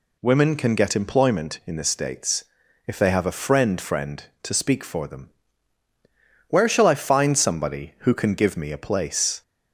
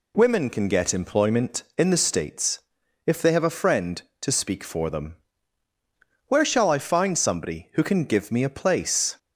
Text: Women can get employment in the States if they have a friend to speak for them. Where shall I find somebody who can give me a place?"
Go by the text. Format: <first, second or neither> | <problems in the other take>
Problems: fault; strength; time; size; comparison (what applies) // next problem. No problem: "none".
second | pauses between "States" and "if"; at 2.4 s; 0.44 s long; noticeable in the second // says "friend" twice; at 3.7 s